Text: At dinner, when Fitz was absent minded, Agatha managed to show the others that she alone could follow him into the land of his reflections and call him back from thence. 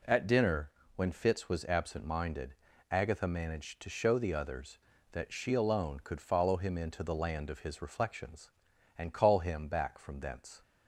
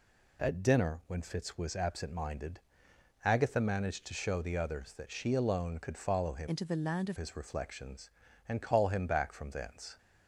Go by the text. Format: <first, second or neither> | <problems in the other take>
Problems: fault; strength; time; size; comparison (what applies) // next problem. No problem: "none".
first | changes voice from "into" to "of"; from 6.4 to 7.1 s; 0.7 s long